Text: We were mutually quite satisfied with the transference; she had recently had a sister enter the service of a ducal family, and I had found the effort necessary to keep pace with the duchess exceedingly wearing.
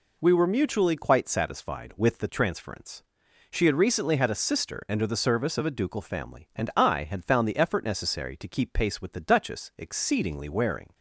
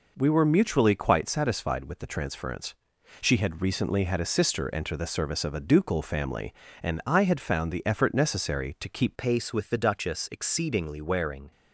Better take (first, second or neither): first